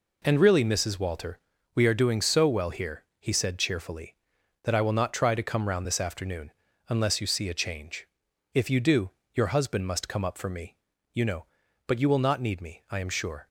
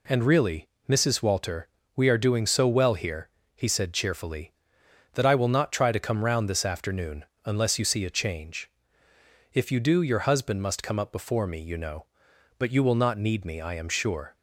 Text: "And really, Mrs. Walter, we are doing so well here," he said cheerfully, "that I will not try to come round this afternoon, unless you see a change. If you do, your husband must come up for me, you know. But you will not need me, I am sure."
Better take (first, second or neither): first